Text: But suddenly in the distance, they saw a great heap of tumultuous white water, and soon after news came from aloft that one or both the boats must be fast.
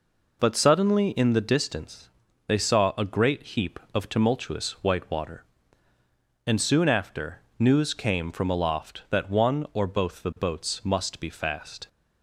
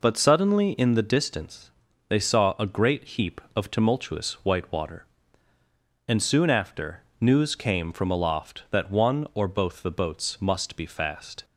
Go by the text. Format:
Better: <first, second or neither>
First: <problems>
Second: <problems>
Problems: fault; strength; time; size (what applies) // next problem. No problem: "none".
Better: neither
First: pauses between "after" and "news"; slight; at 7.4 s; 0.18 s long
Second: pauses between "after" and "news"; slight; at 7.0 s; 0.18 s long